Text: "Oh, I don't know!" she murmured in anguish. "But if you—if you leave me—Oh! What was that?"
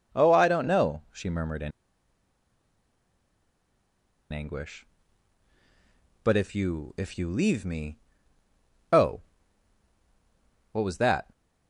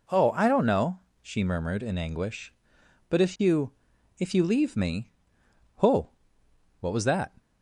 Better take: second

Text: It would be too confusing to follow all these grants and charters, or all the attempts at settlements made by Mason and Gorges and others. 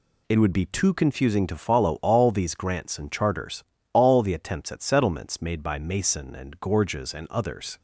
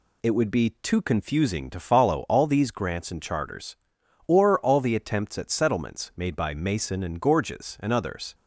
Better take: second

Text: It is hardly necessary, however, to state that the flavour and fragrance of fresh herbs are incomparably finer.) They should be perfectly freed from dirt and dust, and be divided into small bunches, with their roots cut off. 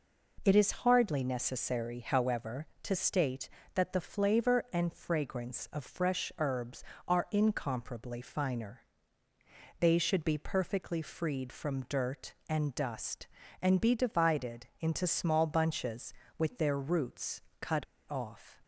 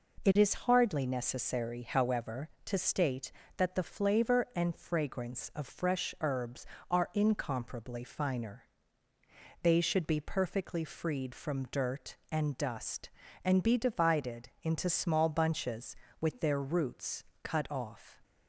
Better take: second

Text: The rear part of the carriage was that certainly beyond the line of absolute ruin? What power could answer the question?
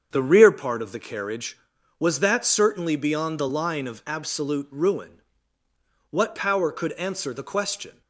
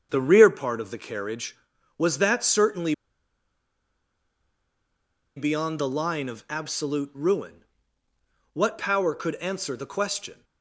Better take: first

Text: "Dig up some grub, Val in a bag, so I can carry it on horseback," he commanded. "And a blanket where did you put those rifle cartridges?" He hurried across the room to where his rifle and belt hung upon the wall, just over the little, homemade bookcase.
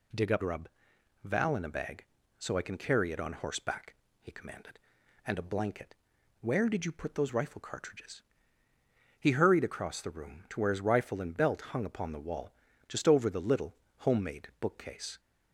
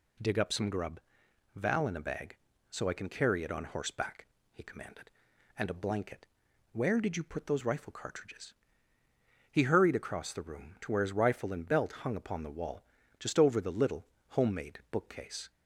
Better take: second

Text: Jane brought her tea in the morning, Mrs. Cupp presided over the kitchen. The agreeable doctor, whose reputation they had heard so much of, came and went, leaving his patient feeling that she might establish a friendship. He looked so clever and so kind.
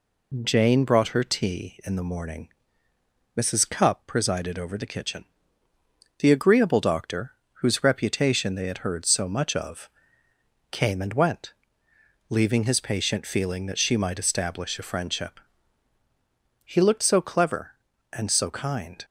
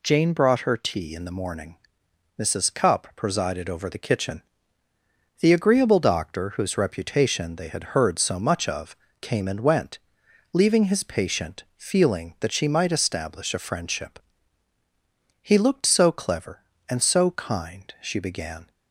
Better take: first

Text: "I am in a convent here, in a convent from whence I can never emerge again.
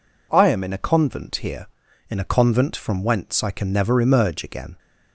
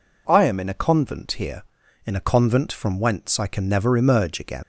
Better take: first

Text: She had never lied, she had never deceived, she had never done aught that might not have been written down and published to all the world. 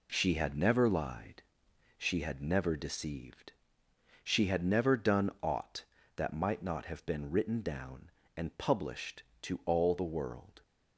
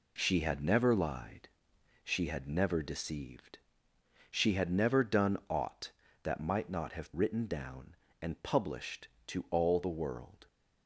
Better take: first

